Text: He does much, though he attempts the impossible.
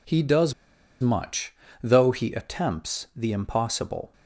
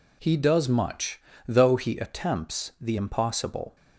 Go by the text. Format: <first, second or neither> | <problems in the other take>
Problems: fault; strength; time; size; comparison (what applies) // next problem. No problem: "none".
second | pauses between "does" and "much"; noticeable; at 0.5 s; 0.48 s long